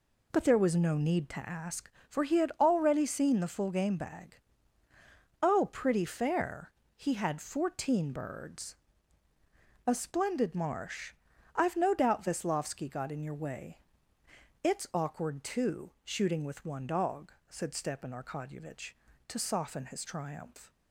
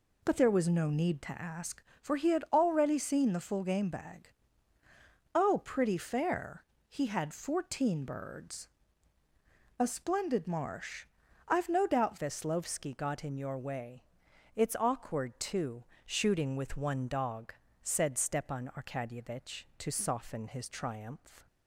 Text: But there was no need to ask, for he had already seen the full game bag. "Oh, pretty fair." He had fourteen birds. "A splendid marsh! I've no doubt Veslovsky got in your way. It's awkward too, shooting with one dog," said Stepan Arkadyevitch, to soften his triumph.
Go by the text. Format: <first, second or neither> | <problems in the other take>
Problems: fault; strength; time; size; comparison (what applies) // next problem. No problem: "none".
first | changes voice at "Veslovsky"; from 12.1 s on; 9.3 s long